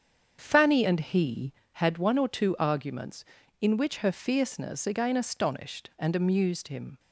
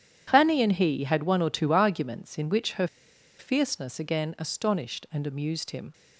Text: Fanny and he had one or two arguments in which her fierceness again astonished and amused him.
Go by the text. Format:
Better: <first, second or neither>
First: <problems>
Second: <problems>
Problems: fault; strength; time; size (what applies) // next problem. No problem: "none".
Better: first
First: starts louder than the rest; strong; until 1.4 s; 7.5 dB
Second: starts louder than the rest; strong; until 1.2 s; 9.5 dB // pauses between "her" and "fierceness"; noticeable; at 2.8 s; 0.52 s long